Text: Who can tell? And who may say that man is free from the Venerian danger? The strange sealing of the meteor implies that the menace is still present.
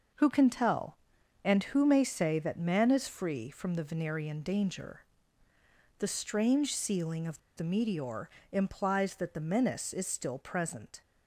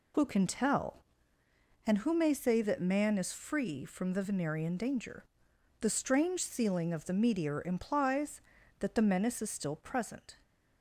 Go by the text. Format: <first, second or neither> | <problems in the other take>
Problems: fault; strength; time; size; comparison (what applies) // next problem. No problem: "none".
second | pauses between "of" and "the"; slight; at 7.3 s; 0.18 s long // pauses between "meteor" and "implies"; slight; at 8.2 s; 0.22 s long